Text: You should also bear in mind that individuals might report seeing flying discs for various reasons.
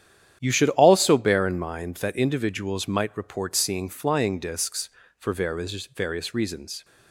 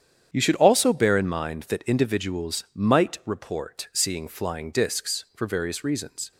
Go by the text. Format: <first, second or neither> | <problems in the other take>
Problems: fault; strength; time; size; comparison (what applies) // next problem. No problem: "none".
second | starts louder than the rest; strong; until 1.4 s; 10 dB; strong in the second // says "various" twice; at 5.8 s